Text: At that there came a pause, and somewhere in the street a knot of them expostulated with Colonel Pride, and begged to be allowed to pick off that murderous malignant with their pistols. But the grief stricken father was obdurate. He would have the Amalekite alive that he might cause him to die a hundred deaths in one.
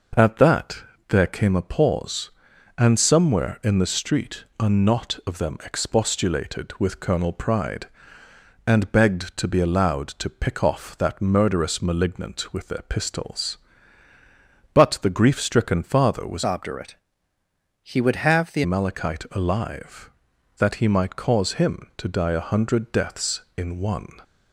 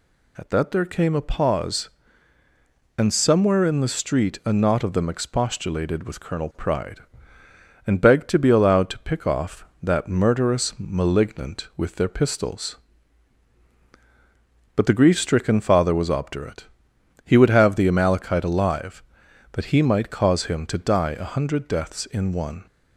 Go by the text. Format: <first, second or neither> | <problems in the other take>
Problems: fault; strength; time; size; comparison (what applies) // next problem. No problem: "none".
second | pauses between "that" and "there"; slight; at 0.8 s; 0.26 s long // pauses between "street" and "a"; slight; at 4.4 s; 0.16 s long // changes voice from "obdurate" to "the"; from 16.4 to 18.6 s; 2.2 s long